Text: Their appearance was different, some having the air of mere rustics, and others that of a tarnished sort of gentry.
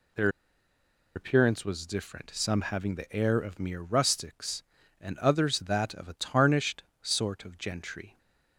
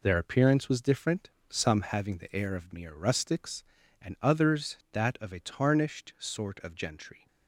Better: second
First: pauses between "Their" and "appearance"; noticeable; at 0.2 s; 0.86 s long // pauses between "tarnished" and "sort"; slight; at 6.8 s; 0.18 s long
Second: none

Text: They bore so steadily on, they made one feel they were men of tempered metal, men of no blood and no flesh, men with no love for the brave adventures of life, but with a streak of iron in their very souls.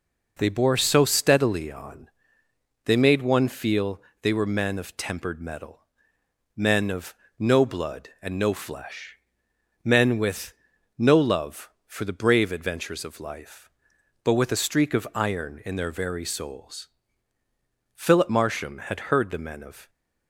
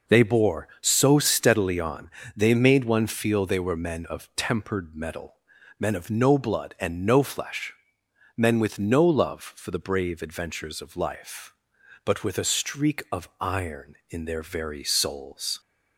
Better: second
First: pauses between "feel" and "they"; slight; at 3.9 s; 0.22 s long // pauses between "of" and "no"; slight; at 7.1 s; 0.24 s long // pauses between "with" and "no"; at 10.5 s; 0.44 s long // goes on to say "Philip Marsham had heard the men of"; strong; from 17.9 s on; 1.9 s long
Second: none

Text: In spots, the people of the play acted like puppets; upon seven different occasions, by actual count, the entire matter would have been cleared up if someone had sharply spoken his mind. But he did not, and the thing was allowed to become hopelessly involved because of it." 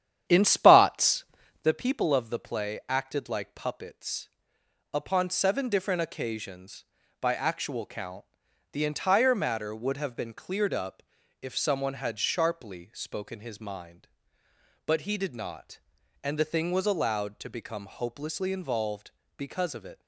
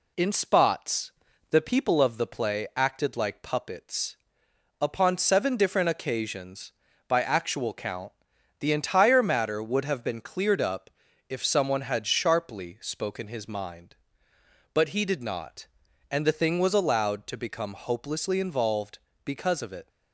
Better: second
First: starts louder than the rest; strong; until 1.7 s; 10 dB // pauses between "up" and "if"; at 11.0 s; 0.40 s long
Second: pauses between "up" and "if"; at 10.8 s; 0.40 s long

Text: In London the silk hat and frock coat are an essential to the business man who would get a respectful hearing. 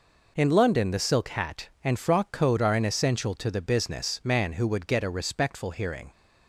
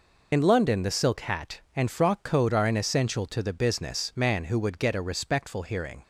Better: first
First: none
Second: loses the start of "In"; at 0.3 s; 45 ms

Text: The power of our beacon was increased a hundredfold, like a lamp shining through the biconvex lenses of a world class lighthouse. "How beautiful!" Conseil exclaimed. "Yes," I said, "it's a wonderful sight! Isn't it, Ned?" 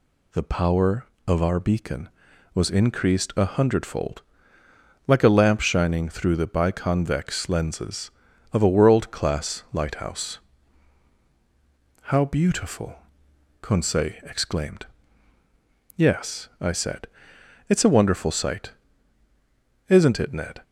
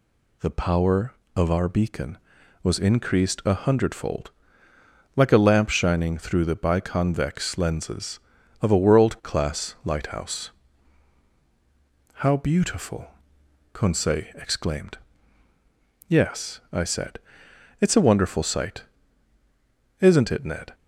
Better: neither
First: none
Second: none

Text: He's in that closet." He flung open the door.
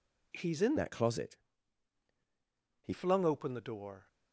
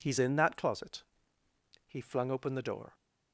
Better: second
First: changes voice from "that" to "He"; from 0.7 to 2.9 s; 2.2 s long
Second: none

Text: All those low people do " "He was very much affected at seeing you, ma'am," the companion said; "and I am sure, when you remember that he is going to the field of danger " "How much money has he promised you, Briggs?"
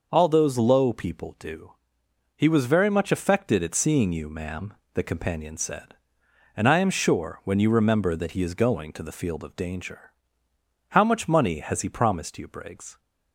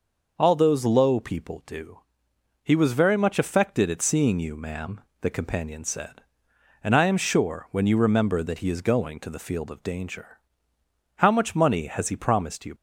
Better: first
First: none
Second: stops before "Briggs"; at 12.7 s

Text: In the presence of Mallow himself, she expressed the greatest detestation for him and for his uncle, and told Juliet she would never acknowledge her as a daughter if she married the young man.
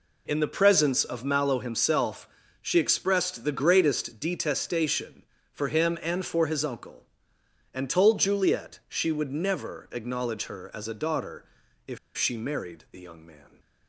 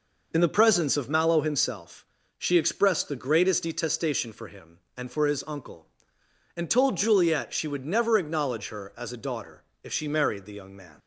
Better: second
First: pauses between "daughter" and "if"; at 11.4 s; 0.42 s long // pauses between "if" and "she"; slight; at 11.9 s; 0.19 s long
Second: pauses between "daughter" and "if"; slight; at 9.6 s; 0.18 s long

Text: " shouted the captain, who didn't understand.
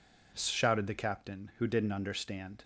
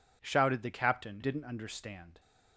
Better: first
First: none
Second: skips "who"; at 1.2 s

